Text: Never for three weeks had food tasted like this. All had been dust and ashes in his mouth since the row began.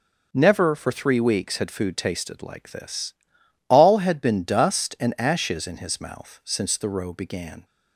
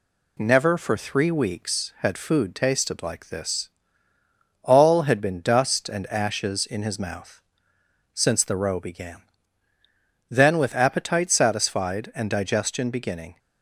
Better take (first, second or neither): first